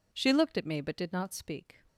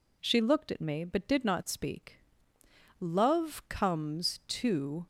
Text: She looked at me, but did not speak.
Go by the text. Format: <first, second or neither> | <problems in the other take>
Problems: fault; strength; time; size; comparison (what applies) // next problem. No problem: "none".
first | goes on to say "Love comes to"; strong; from 3.0 s on; 2.0 s long